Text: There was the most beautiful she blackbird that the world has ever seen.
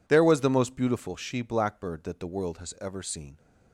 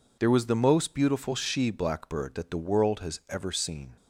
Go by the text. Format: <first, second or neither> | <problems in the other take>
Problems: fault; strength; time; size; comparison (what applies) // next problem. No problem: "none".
neither | none